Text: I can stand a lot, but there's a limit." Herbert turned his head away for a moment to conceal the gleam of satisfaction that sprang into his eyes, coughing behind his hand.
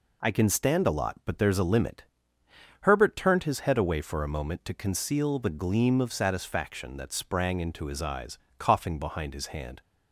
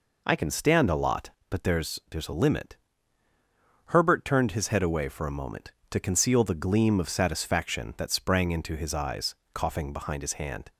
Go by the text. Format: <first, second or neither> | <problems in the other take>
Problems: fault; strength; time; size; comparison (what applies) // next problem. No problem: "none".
first | says "there's" twice; at 2.0 s